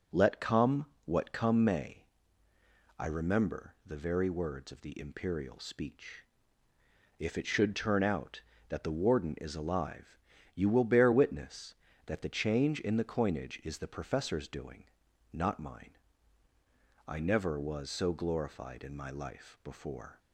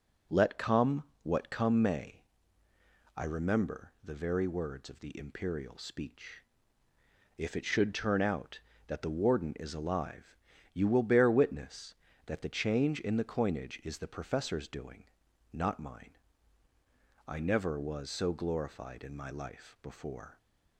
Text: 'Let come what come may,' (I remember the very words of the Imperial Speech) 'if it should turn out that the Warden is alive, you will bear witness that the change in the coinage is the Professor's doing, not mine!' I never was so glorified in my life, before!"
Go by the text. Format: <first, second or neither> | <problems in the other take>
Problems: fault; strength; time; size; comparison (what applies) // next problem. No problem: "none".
neither | pauses between "come" and "what"; slight; the same in both